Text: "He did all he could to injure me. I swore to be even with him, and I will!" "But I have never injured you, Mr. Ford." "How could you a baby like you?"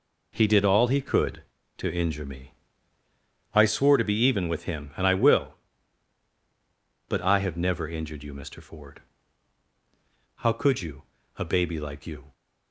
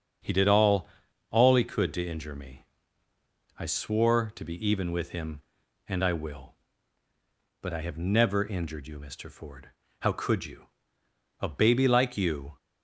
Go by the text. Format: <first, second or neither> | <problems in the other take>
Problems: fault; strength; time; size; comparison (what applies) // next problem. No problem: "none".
first | starts louder than the rest; until 1.6 s; 7 dB // says "all" twice; at 1.3 s // pauses between "you" and "a"; noticeable; at 10.6 s; 0.72 s long; slight in the first